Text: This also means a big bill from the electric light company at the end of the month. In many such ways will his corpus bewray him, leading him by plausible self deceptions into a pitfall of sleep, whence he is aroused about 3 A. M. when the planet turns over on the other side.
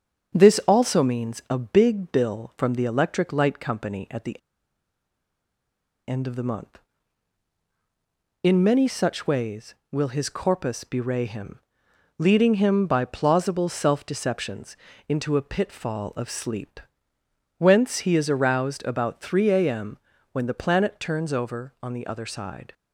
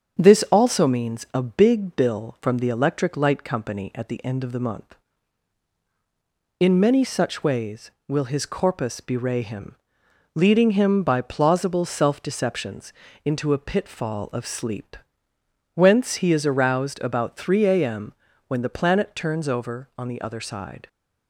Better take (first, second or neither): second